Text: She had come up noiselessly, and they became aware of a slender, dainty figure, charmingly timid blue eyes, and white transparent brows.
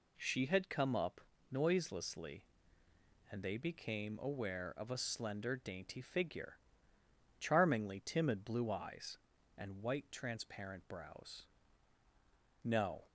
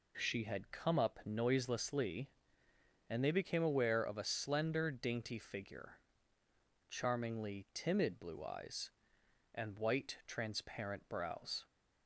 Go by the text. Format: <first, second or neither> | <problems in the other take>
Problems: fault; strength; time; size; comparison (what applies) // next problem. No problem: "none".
second | pauses between "up" and "noiselessly"; slight; at 1.1 s; 0.30 s long // goes on to say "No"; slight; from 12.6 s on; 0.42 s long